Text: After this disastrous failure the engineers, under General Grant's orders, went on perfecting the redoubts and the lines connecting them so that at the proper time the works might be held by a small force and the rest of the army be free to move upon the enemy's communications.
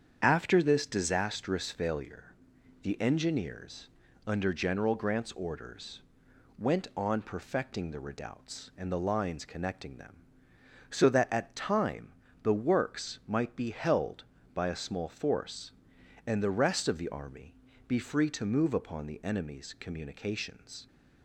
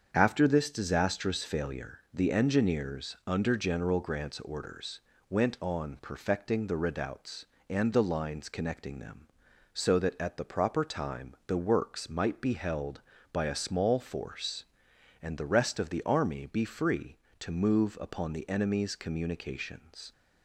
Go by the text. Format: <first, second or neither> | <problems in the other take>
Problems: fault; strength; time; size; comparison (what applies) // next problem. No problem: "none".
second | starts louder than the rest; strong; until 1.2 s; 8 dB; strong in the second // pauses between "failure" and "the"; noticeable; at 2.3 s; 0.50 s long // skips "the proper"; at 11.5 s // pauses between "time" and "the"; slight; at 12.1 s; 0.28 s long // pauses between "army" and "be"; slight; at 17.5 s; 0.32 s long